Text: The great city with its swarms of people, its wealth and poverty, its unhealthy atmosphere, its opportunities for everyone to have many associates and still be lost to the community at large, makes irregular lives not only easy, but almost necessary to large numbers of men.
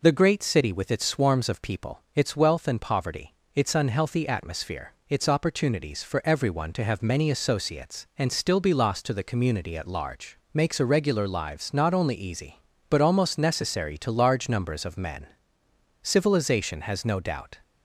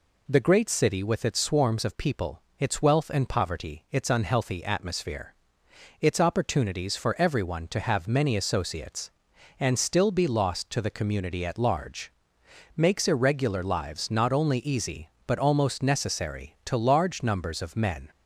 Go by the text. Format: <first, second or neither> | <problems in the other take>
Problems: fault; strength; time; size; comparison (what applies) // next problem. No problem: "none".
second | goes on to say "Civilization has no doubt"; from 16.0 s on; 1.5 s long